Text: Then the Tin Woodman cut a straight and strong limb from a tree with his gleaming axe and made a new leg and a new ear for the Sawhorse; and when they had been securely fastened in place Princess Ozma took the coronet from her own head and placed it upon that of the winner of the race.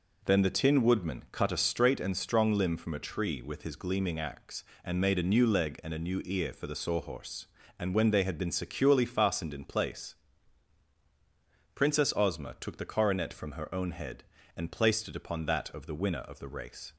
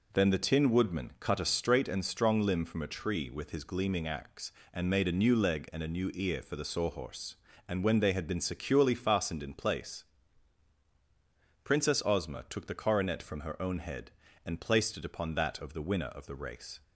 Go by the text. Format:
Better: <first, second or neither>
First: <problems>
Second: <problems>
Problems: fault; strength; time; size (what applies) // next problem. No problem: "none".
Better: neither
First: pauses between "place" and "Princess"; strong; at 10.1 s; 1.6 s long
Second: pauses between "place" and "Princess"; strong; at 10.0 s; 1.6 s long